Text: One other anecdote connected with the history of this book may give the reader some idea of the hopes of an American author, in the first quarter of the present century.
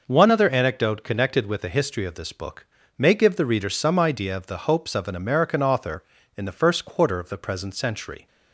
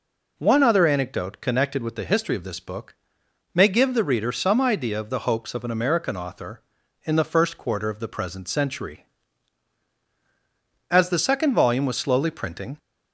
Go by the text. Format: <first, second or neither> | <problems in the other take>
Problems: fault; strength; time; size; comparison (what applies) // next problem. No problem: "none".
first | pauses between "book" and "may"; noticeable; at 2.9 s; 0.58 s long; slight in the first // goes on to say "As the second volume was slowly printing"; strong; from 10.8 s on; 1.8 s long